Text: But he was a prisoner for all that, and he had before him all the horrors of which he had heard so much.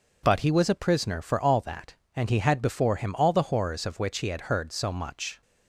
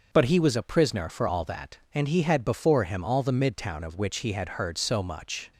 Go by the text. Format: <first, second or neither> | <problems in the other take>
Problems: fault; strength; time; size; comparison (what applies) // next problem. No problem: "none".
first | starts louder than the rest; noticeable; until 1.1 s; 6 dB // says "midtown" for "horrors"; at 3.3 s